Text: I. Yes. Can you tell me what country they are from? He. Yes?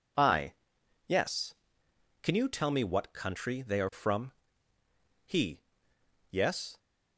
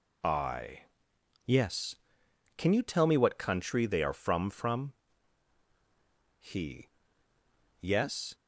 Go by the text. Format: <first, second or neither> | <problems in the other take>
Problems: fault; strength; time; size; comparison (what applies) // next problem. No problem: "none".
first | says "from" twice; at 4.5 s